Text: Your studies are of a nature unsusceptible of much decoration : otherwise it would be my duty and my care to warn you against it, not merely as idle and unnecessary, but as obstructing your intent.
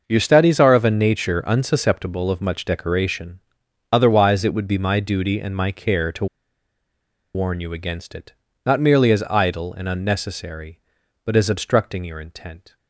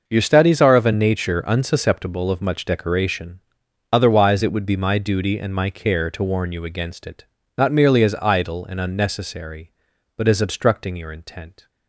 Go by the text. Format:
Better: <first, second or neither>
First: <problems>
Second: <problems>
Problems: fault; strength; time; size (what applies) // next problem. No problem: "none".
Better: second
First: pauses between "to" and "warn"; at 6.2 s; 1.0 s long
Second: none